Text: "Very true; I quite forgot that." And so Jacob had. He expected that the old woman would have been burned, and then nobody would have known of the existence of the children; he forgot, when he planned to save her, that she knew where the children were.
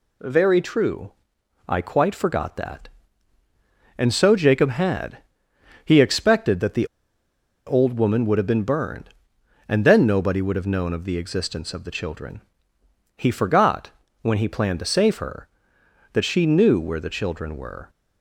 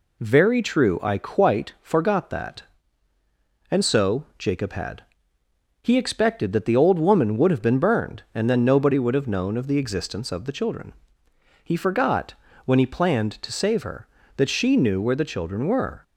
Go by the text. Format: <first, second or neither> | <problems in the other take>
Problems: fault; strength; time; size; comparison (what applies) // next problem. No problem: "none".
second | pauses between "the" and "old"; noticeable; at 6.8 s; 0.80 s long